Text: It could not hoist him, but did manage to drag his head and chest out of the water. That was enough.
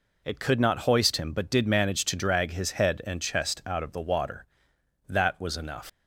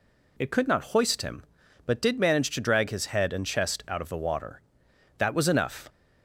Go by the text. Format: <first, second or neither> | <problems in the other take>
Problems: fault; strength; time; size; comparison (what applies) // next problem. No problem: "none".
second | leaves "enough" unfinished; at 5.8 s; 90 ms